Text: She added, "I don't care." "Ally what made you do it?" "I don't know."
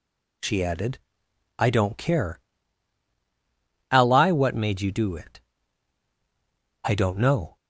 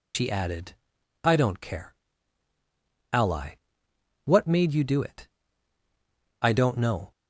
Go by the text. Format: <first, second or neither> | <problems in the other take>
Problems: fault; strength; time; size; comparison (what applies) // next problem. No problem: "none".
first | loses the start of "She"; at 0.1 s; 85 ms // pauses between "Ally" and "what"; noticeable; at 3.5 s; 0.68 s long